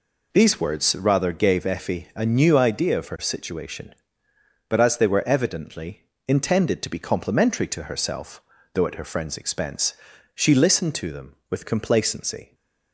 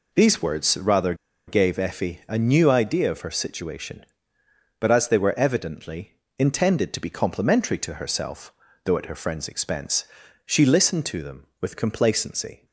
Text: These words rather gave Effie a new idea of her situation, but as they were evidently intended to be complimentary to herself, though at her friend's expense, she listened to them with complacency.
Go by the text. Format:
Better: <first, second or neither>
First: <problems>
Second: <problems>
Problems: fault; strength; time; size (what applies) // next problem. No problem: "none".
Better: first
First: pauses between "evidently" and "intended"; slight; at 6.0 s; 0.22 s long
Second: pauses between "rather" and "gave"; slight; at 1.1 s; 0.33 s long // pauses between "evidently" and "intended"; slight; at 6.1 s; 0.22 s long